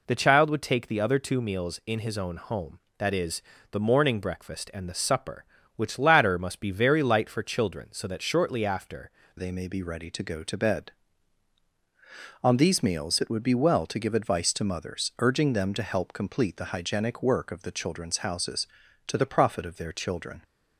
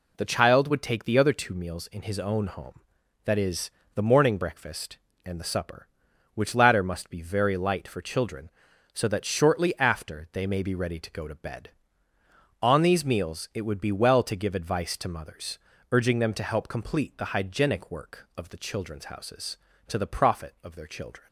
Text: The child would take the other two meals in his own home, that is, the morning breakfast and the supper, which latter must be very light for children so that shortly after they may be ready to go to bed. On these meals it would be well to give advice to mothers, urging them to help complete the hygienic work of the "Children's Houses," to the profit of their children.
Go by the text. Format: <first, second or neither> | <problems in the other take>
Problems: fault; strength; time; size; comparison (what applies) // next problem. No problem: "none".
second | changes voice at "they"; from 9.3 s on; 11.1 s long